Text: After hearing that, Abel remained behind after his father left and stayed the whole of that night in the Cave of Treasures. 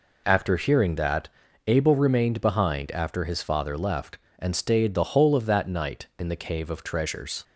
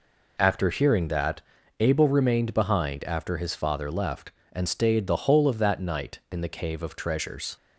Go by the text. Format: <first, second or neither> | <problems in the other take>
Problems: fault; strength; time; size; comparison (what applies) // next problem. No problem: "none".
neither | none